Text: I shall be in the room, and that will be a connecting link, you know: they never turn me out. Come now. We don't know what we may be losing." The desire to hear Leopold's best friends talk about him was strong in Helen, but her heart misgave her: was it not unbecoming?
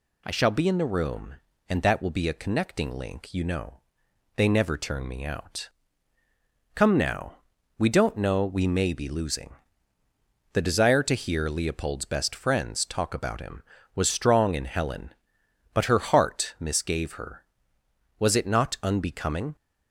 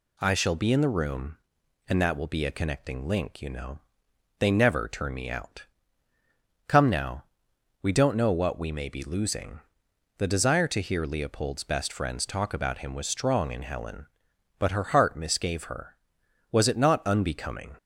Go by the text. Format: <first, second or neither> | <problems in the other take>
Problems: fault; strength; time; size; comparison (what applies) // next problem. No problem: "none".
second | skips "what"; at 8.4 s